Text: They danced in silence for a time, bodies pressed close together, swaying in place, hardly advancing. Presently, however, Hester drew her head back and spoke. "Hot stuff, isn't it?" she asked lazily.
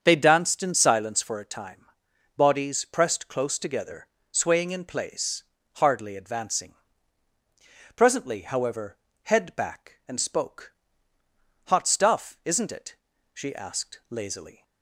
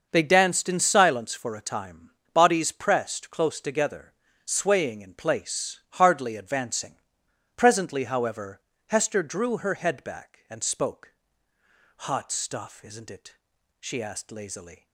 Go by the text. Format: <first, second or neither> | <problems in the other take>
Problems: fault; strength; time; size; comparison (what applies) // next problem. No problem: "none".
second | starts louder than the rest; strong; until 1.0 s; 7 dB; noticeable in the second // skips "Hester drew her"; at 9.1 s